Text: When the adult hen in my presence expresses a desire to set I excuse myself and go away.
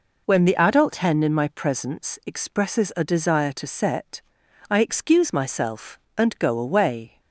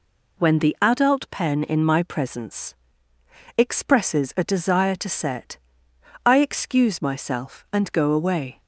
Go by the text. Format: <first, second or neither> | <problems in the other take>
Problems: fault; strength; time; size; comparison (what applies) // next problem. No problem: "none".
first | says "pen" for "hen"; at 1.3 s // pauses between "presence" and "expresses"; noticeable; at 2.7 s; 0.80 s long // pauses between "set" and "I"; noticeable; at 5.5 s; 0.68 s long; noticeable in the first